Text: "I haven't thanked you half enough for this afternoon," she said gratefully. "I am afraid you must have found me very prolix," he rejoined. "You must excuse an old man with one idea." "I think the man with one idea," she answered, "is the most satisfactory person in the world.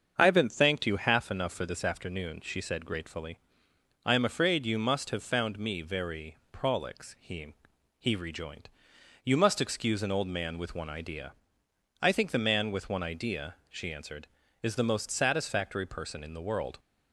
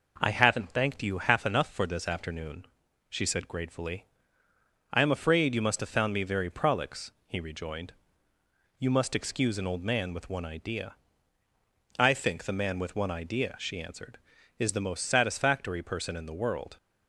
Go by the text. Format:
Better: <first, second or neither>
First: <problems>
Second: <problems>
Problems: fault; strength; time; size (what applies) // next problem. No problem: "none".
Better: second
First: starts louder than the rest; until 1.1 s; 6.5 dB // pauses between "very" and "prolix"; slight; at 6.3 s; 0.16 s long // says "he" twice; at 7.9 s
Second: none